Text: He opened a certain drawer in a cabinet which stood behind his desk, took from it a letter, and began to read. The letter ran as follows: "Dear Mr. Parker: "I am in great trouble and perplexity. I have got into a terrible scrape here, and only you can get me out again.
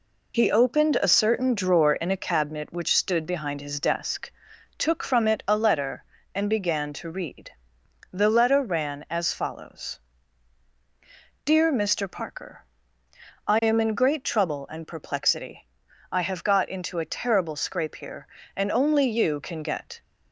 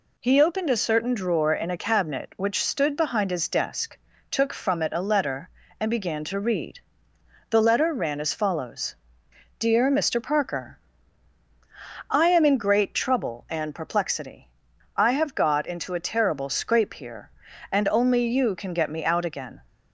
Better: second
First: stops before "me out again"; at 20.0 s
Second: none

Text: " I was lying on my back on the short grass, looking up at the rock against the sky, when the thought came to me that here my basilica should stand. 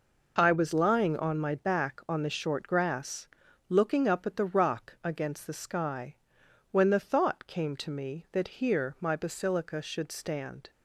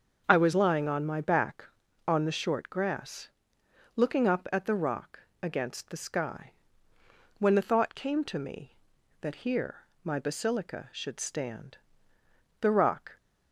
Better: first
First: none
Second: starts louder than the rest; until 1.2 s; 6.5 dB // pauses between "rock" and "against"; slight; at 5.1 s; 0.22 s long // pauses between "here" and "my"; slight; at 9.8 s; 0.22 s long // goes on to say "The rock"; from 12.6 s on; 0.56 s long

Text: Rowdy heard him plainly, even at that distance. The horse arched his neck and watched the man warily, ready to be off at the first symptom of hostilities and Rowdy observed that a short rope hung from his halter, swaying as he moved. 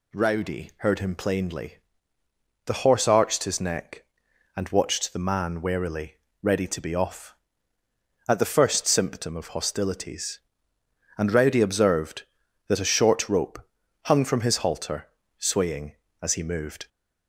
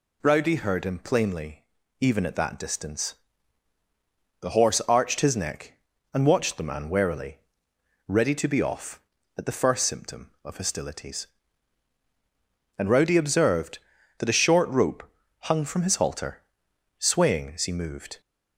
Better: second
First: skips "even at that distance"; at 2.2 s // pauses between "rope" and "hung"; at 13.5 s; 0.44 s long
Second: pauses between "rope" and "hung"; slight; at 15.0 s; 0.34 s long

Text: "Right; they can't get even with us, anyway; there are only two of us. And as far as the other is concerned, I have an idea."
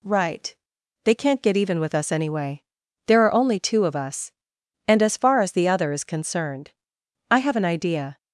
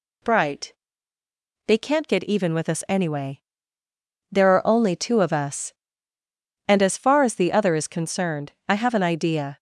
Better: first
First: none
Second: says "Bright" for "Right"; at 0.2 s

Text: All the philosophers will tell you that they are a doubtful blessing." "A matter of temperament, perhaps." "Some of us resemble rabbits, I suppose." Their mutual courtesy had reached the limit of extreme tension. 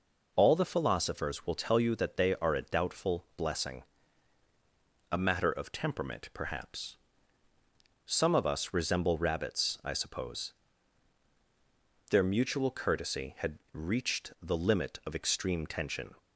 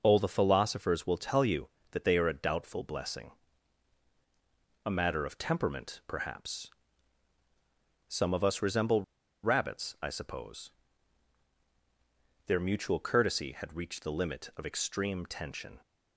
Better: first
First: none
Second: pauses between "resemble" and "rabbits"; at 9.0 s; 0.41 s long

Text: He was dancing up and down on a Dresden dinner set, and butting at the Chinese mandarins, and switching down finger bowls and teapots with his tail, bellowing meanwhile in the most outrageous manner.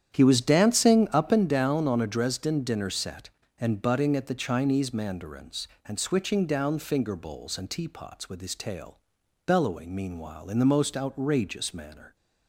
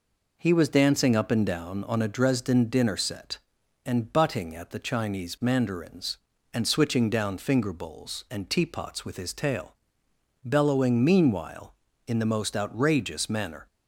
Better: second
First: starts louder than the rest; strong; until 1.5 s; 9.5 dB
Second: none

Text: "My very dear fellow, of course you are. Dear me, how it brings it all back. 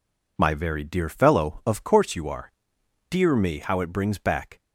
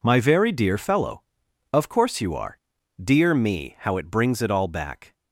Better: second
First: skips "it all"; at 4.1 s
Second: none

